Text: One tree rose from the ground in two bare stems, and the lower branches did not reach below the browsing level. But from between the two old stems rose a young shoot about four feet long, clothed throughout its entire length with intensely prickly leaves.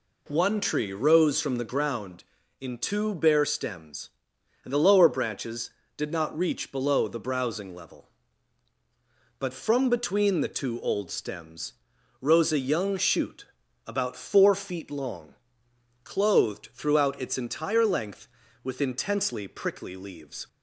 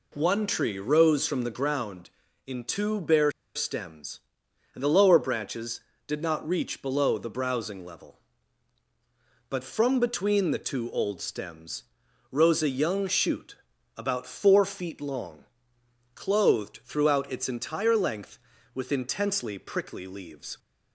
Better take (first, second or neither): first